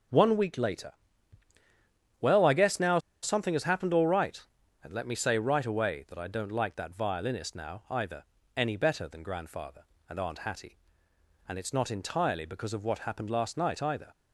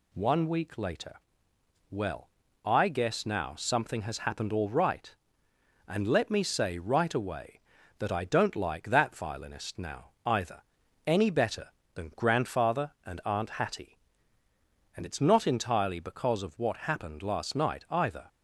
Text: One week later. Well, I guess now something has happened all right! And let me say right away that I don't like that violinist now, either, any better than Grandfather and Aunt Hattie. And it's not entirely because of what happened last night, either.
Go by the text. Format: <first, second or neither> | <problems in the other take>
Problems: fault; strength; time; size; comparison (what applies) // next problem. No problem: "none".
second | starts louder than the rest; until 2.3 s; 6.5 dB // pauses between "now" and "something"; slight; at 2.9 s; 0.24 s long